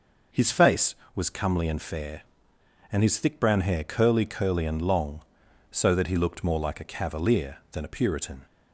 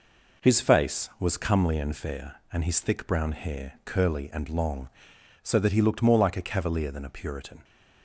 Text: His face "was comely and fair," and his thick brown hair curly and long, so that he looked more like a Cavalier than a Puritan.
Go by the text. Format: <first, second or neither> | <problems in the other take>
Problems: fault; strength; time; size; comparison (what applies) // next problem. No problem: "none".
second | says "curly" twice; at 4.2 s